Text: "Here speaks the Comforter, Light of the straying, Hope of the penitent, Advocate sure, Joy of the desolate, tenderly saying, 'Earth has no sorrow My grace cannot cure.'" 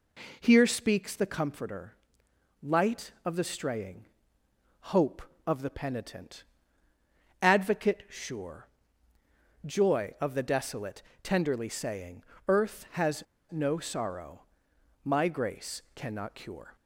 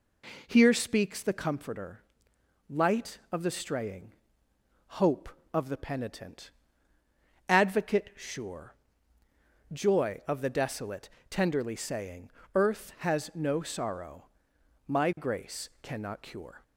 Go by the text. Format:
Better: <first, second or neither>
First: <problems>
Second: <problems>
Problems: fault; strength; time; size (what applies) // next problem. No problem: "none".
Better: second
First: pauses between "has" and "no"; slight; at 13.2 s; 0.27 s long // pauses between "sorrow" and "My"; noticeable; at 14.4 s; 0.60 s long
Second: pauses between "sorrow" and "My"; noticeable; at 14.2 s; 0.60 s long